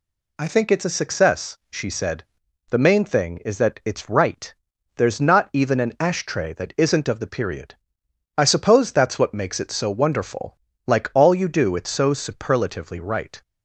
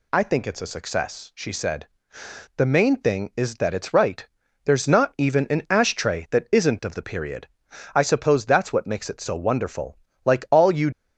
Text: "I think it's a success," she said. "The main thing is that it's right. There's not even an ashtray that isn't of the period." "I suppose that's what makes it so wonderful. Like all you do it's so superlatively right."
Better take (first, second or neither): first